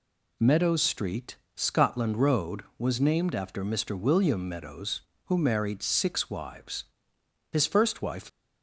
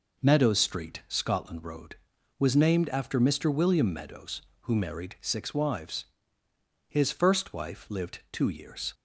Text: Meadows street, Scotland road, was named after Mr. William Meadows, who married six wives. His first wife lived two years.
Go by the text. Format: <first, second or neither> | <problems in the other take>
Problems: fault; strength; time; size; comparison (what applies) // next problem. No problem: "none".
second | stops before "lived two years"; at 8.2 s